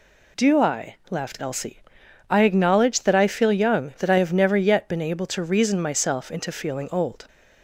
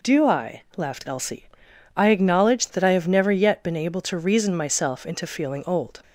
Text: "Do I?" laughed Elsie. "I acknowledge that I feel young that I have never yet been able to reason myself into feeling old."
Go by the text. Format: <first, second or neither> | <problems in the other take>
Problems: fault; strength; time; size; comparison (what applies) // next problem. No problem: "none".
first | skips "that I feel young"; at 2.7 s